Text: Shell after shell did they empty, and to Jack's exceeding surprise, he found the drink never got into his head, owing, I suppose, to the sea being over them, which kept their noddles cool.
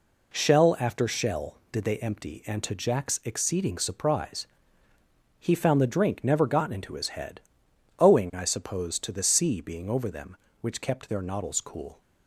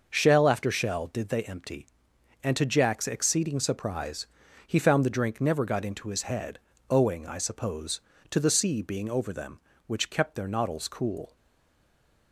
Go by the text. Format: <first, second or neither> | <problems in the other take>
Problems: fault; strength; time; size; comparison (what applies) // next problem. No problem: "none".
first | starts louder than the rest; noticeable; until 1.1 s; 6 dB // stays silent after the last word; from 11.3 s on; 1.0 s long